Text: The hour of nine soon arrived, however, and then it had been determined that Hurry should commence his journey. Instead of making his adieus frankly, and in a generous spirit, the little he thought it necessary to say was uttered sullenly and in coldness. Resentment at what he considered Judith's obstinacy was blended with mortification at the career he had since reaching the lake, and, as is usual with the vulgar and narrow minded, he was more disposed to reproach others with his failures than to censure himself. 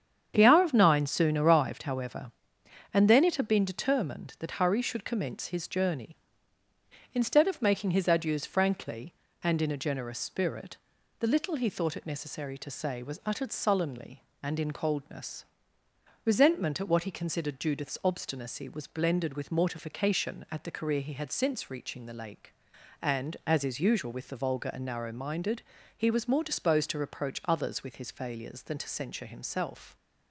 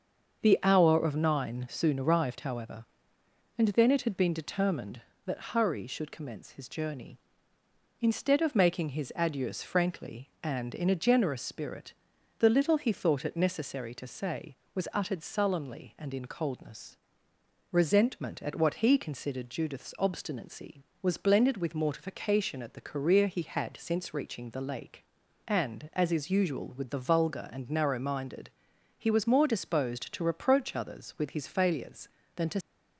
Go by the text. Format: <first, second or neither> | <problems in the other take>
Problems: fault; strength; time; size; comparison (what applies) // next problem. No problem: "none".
first | starts louder than the rest; until 1.4 s; 6.5 dB; strong in the first // stops before "censure himself"; at 32.6 s